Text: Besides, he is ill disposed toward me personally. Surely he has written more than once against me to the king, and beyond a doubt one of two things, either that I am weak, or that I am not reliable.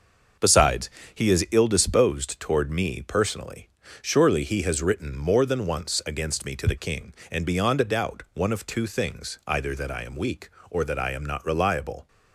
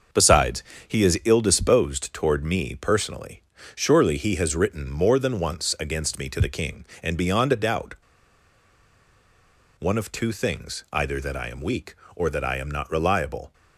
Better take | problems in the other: first | starts louder than the rest; until 1.4 s; 6 dB; also in the first // pauses between "doubt" and "one"; strong; at 7.9 s; 1.8 s long

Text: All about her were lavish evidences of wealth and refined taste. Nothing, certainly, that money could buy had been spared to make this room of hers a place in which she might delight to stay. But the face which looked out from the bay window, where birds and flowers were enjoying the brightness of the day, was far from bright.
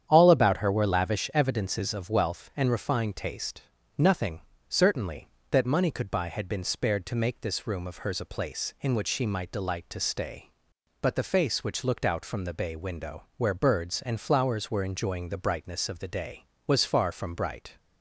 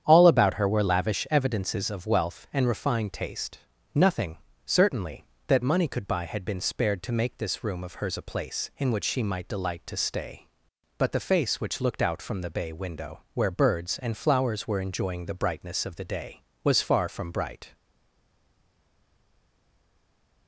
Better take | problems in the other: first | starts louder than the rest; strong; until 1.0 s; 9 dB; strong in the first // stays silent after the last word; strong; from 17.7 s on; 2.7 s long

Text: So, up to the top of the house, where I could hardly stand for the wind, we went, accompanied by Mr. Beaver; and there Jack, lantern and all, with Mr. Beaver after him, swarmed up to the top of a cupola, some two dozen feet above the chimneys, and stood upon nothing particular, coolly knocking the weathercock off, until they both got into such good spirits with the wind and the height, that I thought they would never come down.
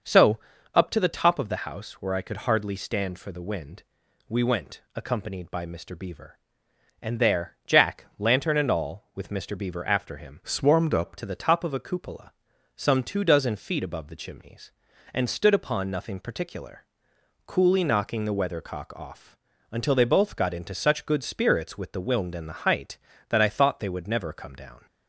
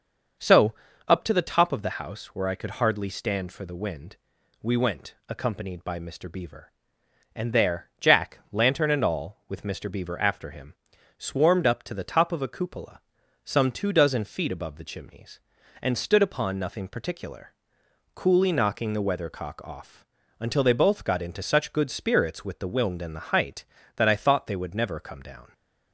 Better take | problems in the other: second | starts louder than the rest; until 1.4 s; 6.5 dB; also in the second // changes voice from "swarmed" to "up"; from 10.4 to 11.1 s; 0.7 s long

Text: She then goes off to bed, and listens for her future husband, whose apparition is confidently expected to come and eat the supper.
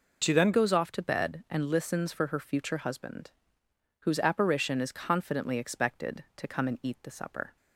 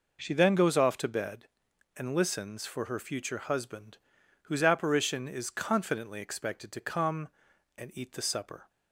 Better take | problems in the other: second | changes voice at "goes"; from 0.5 s on; 7.0 s long

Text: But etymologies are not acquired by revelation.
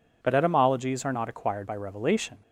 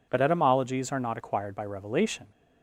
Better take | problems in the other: neither | none

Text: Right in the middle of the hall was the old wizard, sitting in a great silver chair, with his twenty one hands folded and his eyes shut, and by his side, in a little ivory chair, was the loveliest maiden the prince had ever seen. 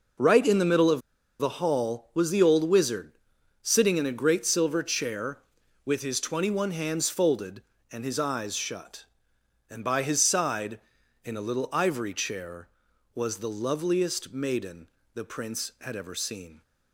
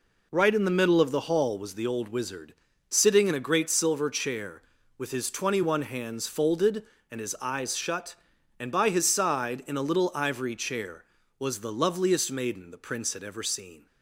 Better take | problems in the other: second | pauses between "of" and "the"; at 1.0 s; 0.39 s long // pauses between "maiden" and "the"; slight; at 14.8 s; 0.26 s long

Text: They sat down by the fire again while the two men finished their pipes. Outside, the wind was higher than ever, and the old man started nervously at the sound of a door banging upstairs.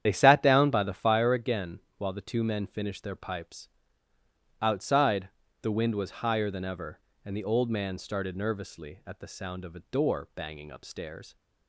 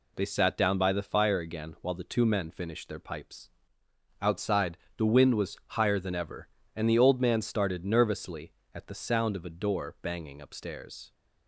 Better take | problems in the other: second | loses the start of "They"; at 0.0 s; 60 ms // starts louder than the rest; strong; until 1.0 s; 9.5 dB // pauses between "again" and "while"; slight; at 1.7 s; 0.18 s long

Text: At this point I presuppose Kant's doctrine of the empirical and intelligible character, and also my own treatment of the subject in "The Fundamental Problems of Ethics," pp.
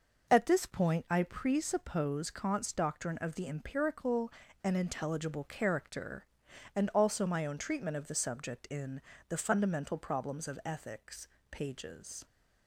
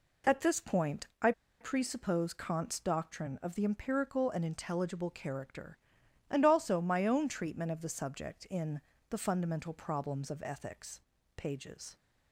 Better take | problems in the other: first | pauses between "point" and "I"; slight; at 1.0 s; 0.16 s long // pauses between "I" and "presuppose"; slight; at 1.3 s; 0.29 s long // pauses between "in" and "The"; slight; at 8.8 s; 0.26 s long; slight in the first

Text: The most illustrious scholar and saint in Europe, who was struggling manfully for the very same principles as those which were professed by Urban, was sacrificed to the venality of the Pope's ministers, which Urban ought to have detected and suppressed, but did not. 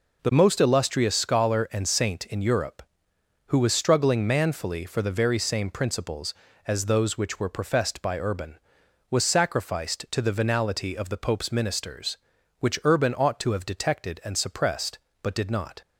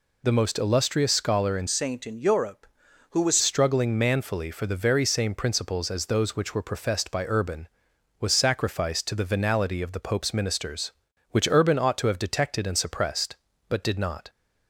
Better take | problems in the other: first | changes voice from "saint" to "was"; from 1.6 to 3.3 s; 1.7 s long

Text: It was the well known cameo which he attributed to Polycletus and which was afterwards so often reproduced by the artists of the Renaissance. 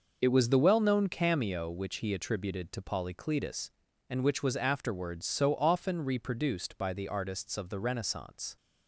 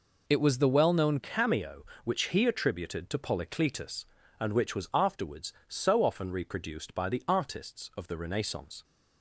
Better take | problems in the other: first | changes voice at "cameo"; from 1.1 s on; 7.7 s long

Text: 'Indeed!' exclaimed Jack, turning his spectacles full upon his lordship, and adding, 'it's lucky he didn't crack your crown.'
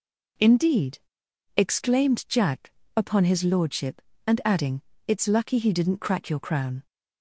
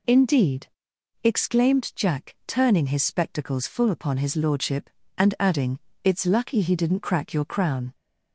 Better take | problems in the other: second | skips "turning his spectacles full"; at 2.8 s

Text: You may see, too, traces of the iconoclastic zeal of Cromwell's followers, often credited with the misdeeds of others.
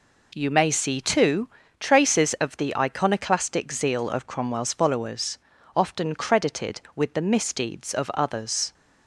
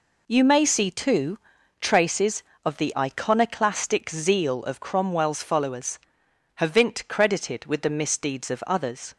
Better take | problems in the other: first | says "havint" for "often"; at 6.5 s

